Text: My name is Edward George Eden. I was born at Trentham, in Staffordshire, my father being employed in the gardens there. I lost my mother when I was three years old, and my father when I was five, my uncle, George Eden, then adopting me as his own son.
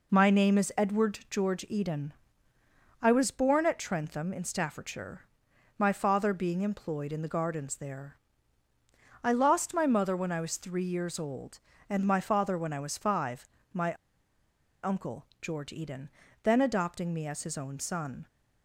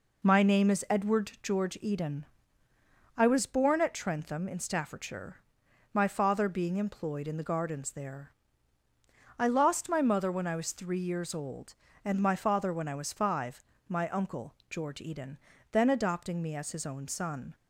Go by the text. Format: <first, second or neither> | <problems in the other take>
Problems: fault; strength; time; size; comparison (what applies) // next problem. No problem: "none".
second | pauses between "my" and "uncle"; noticeable; at 13.9 s; 0.89 s long